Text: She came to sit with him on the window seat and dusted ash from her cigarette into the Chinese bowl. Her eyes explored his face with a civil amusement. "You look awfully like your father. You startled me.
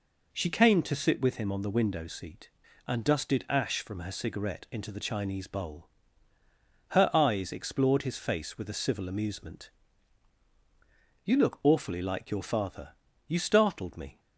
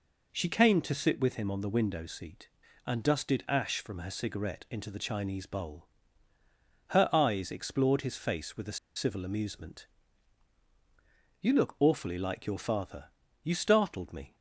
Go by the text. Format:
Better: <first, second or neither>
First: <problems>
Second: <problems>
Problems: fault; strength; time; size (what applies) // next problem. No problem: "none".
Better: first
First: none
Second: pauses between "a" and "civil"; slight; at 8.7 s; 0.18 s long